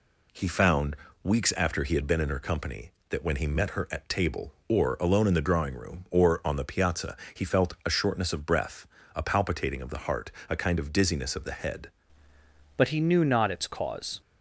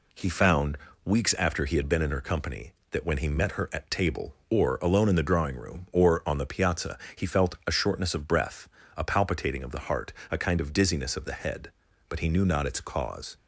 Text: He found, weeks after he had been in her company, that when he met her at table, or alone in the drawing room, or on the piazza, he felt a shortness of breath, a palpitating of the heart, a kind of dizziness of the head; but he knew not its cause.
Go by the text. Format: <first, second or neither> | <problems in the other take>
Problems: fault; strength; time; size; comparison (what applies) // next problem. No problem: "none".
second | changes voice at "but"; from 12.7 s on; 1.5 s long